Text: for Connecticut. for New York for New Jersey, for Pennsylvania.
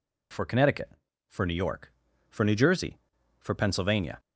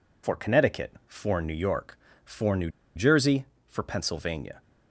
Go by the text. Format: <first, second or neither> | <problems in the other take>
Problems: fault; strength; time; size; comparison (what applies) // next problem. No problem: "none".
first | pauses between "New" and "Jersey"; slight; at 2.7 s; 0.25 s long